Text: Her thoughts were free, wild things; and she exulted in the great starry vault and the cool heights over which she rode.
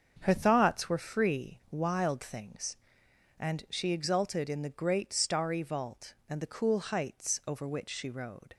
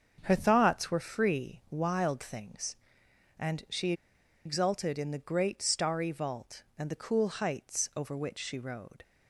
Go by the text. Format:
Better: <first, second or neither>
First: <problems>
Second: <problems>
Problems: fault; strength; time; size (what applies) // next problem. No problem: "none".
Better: first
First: starts louder than the rest; until 1.2 s; 7 dB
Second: starts louder than the rest; until 1.2 s; 7 dB // pauses between "she" and "exulted"; noticeable; at 3.9 s; 0.52 s long